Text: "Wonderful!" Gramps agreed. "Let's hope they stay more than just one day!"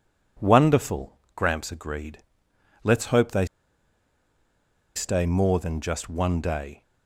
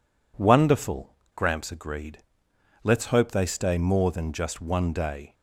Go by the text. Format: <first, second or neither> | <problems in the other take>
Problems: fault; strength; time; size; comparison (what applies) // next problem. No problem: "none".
second | pauses between "they" and "stay"; strong; at 3.4 s; 1.5 s long